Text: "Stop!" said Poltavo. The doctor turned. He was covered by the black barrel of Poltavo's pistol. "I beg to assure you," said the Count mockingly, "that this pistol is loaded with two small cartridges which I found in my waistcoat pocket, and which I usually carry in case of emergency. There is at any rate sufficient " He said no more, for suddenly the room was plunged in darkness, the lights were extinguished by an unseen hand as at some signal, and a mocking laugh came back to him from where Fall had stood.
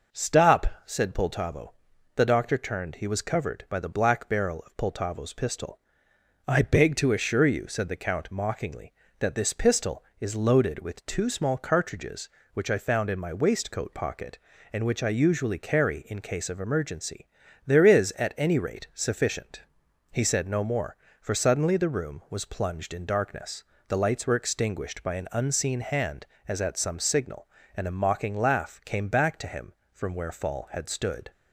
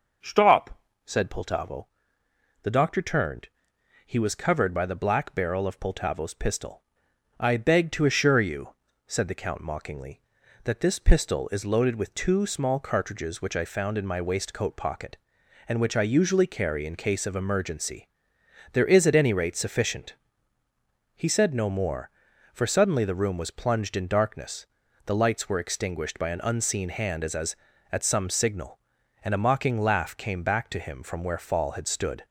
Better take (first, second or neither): first